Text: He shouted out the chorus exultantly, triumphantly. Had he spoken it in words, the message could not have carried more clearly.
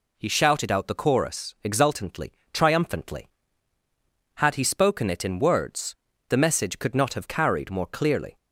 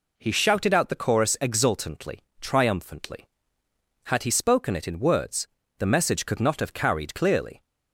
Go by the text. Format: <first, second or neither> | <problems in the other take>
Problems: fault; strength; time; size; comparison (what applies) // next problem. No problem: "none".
first | skips "more"; at 7.1 s